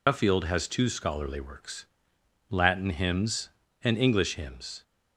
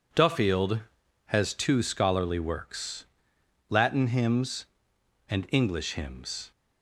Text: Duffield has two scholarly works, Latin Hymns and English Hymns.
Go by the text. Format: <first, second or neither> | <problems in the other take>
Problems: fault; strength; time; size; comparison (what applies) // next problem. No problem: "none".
second | loses the start of "Duffield"; at 0.0 s; 90 ms